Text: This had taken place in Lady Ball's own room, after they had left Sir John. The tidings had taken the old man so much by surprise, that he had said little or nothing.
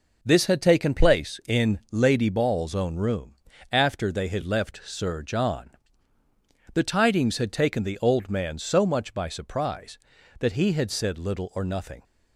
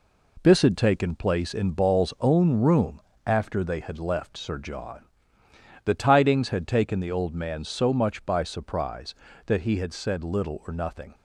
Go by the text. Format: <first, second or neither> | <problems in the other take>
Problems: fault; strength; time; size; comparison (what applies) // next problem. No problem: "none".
first | skips "Lady"; at 1.7 s